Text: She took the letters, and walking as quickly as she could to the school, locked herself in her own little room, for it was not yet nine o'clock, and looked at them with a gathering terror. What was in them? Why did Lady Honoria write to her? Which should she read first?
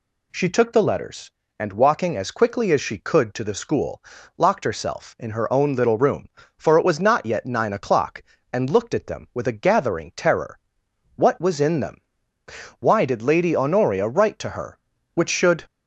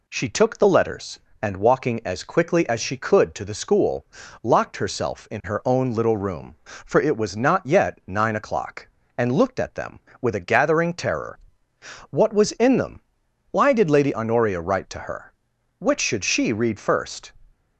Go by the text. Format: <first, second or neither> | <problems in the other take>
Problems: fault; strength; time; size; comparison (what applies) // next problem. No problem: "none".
second | stops before "she read first"; at 15.6 s